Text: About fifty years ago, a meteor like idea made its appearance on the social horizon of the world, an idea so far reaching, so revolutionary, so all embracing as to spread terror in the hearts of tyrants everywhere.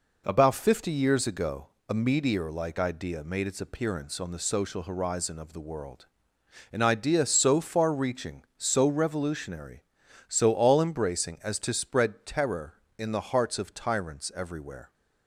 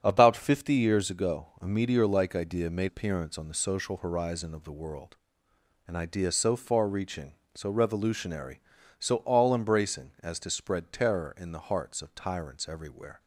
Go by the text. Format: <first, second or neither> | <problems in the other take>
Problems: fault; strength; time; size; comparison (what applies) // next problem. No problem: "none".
first | starts louder than the rest; strong; until 1.0 s; 7.5 dB // skips "its"; at 2.8 s